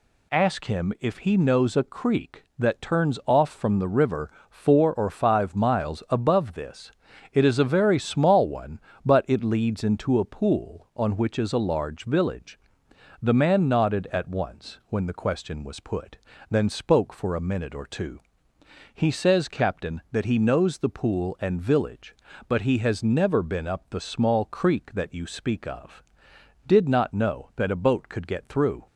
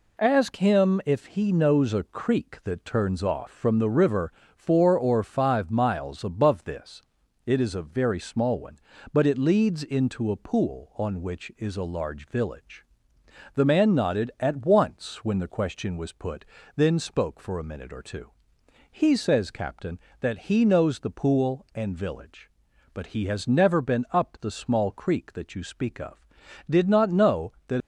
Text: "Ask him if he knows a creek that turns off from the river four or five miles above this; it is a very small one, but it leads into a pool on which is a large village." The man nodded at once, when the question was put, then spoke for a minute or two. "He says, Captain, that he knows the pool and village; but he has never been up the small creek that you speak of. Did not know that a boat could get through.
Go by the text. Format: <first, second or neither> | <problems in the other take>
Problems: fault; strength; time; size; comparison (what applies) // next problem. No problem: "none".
first | pauses between "river" and "four"; slight; at 4.3 s; 0.22 s long; slight in the first // stops before "a boat could get through"; at 27.8 s